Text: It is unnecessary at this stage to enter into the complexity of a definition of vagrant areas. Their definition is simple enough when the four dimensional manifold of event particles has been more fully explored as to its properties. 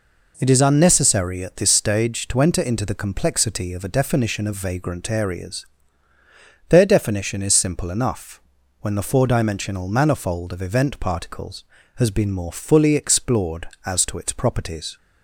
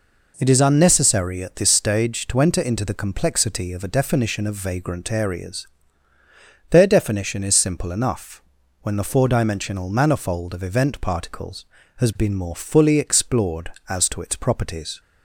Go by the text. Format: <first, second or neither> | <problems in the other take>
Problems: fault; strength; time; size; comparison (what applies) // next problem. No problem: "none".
neither | pauses between "enough" and "when"; the same in both